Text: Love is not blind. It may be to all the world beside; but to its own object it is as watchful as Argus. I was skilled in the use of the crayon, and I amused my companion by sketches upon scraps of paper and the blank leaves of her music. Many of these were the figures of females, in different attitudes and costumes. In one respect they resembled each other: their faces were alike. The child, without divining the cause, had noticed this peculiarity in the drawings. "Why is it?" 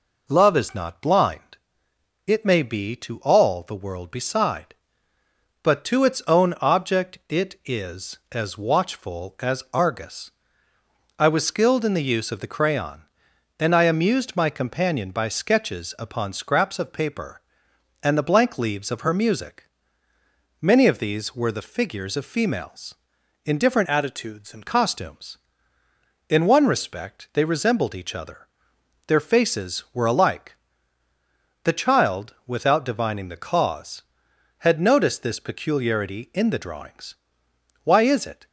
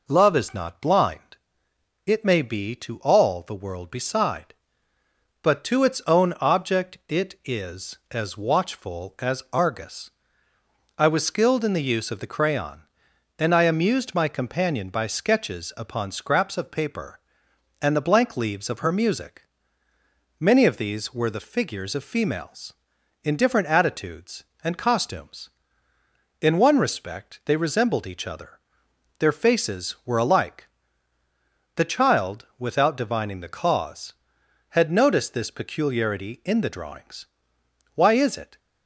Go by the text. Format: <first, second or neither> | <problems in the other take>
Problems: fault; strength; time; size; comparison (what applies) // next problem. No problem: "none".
second | changes voice from "attitudes" to "and"; from 23.8 to 24.6 s; 0.8 s long